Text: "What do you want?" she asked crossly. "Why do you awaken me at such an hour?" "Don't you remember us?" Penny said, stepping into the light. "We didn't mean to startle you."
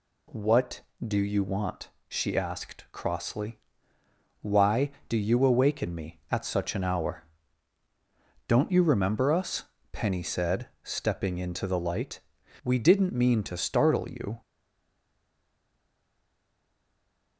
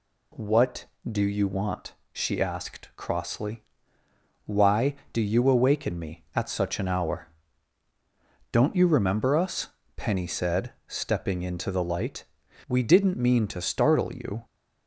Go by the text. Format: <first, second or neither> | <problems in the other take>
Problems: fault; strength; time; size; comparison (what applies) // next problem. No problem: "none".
second | stays silent after the last word; strong; from 14.4 s on; 2.9 s long